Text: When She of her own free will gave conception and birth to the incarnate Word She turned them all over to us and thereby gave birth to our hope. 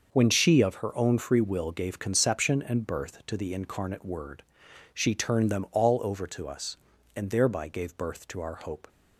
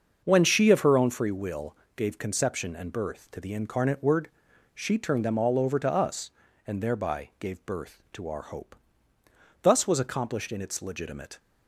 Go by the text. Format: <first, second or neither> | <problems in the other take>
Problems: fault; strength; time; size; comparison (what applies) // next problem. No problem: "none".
first | starts louder than the rest; until 1.2 s; 6.5 dB; also in the first // pauses between "will" and "gave"; slight; at 1.7 s; 0.22 s long // pauses between "Word" and "She"; at 4.2 s; 0.44 s long; noticeable in the first // goes on to say "Thus was accomplished in its legitimate"; strong; from 9.6 s on; 1.7 s long